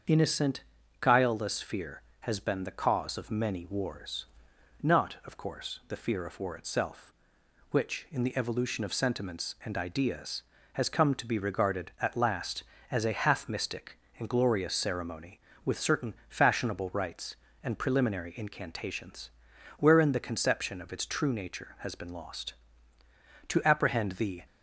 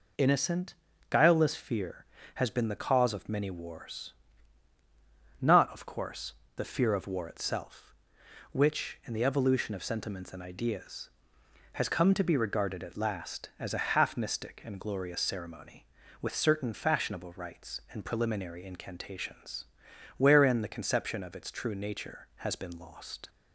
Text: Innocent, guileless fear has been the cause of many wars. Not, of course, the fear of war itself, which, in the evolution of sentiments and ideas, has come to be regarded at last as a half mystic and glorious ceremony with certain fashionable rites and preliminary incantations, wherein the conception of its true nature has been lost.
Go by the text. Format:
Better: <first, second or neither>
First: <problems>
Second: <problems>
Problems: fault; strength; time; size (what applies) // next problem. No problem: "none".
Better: second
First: starts louder than the rest; until 1.4 s; 7 dB // goes on to say "To apprehend the"; noticeable; from 23.4 s on; 0.96 s long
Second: none